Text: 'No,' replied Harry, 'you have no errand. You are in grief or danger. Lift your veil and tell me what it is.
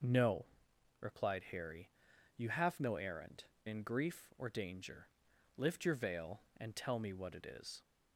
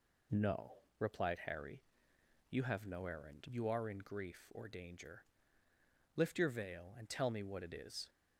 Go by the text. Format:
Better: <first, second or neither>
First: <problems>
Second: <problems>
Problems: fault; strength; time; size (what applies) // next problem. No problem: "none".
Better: second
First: skips "You are"; at 3.5 s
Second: none